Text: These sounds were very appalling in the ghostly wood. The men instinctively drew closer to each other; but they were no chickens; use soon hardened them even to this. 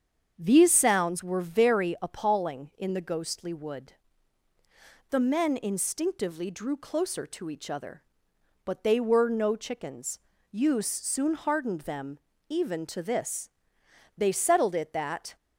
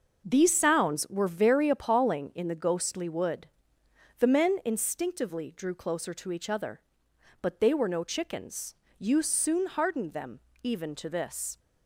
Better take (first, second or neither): second